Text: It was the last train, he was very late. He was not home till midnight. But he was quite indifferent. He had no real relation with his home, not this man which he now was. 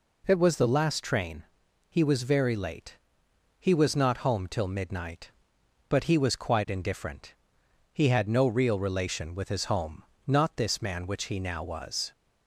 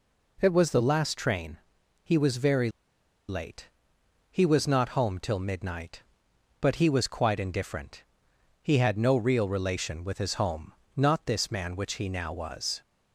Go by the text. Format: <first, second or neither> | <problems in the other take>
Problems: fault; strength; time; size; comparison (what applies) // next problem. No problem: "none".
first | pauses between "very" and "late"; noticeable; at 2.6 s; 0.59 s long